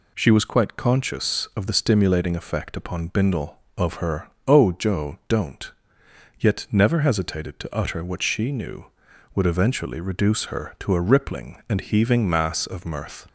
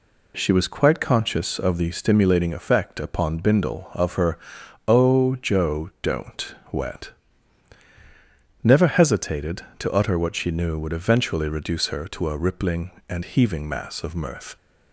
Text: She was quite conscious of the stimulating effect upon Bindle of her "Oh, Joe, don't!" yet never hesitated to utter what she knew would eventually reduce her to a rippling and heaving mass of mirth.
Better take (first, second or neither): first